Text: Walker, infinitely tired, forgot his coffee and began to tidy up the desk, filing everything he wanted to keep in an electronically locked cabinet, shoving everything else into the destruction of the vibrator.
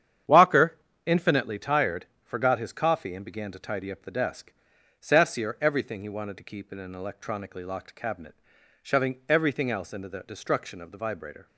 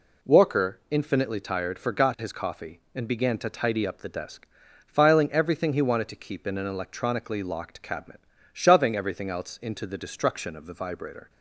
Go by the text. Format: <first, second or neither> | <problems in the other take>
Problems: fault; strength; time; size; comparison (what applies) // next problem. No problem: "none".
second | starts louder than the rest; strong; until 1.5 s; 9 dB // says "sassier" for "filing"; at 4.9 s